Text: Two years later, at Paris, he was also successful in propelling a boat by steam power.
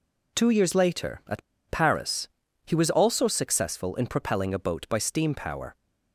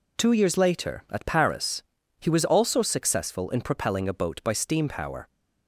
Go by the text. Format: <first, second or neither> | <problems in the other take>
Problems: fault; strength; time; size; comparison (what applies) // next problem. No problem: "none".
second | pauses between "at" and "Paris"; slight; at 1.4 s; 0.27 s long